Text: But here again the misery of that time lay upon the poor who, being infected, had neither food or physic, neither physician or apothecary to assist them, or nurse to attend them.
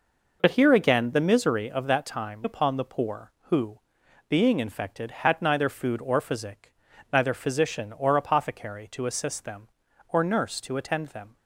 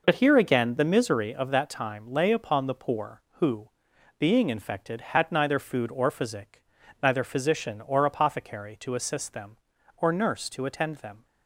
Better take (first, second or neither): second